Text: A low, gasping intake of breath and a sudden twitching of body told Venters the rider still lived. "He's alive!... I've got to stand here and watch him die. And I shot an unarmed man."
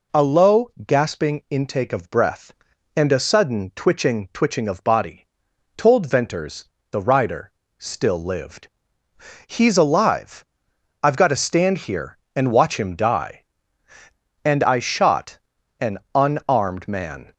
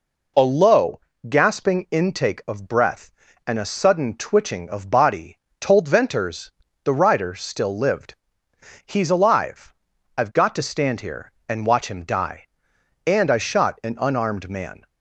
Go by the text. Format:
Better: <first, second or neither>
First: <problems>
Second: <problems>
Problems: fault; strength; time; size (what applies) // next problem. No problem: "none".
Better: second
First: says "twitching" twice; at 4.3 s // pauses between "body" and "told"; noticeable; at 5.2 s; 0.50 s long // pauses between "Venters" and "the"; slight; at 6.6 s; 0.26 s long // pauses between "rider" and "still"; slight; at 7.5 s; 0.26 s long // pauses between "shot" and "an"; at 15.3 s; 0.42 s long // pauses between "an" and "unarmed"; slight; at 15.9 s; 0.16 s long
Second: pauses between "body" and "told"; slight; at 5.3 s; 0.22 s long // pauses between "Venters" and "the"; slight; at 6.5 s; 0.32 s long